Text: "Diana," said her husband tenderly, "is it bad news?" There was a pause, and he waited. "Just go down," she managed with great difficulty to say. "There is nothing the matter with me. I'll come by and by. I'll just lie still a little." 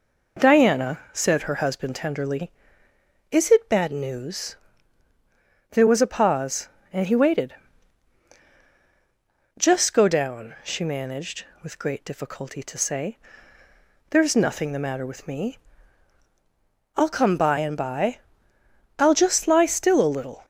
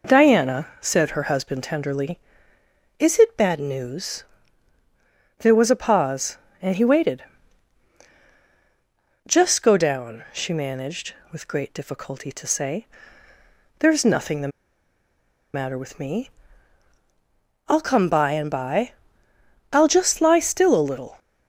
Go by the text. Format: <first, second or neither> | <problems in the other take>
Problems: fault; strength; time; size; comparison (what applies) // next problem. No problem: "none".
first | pauses between "the" and "matter"; at 14.5 s; 1.0 s long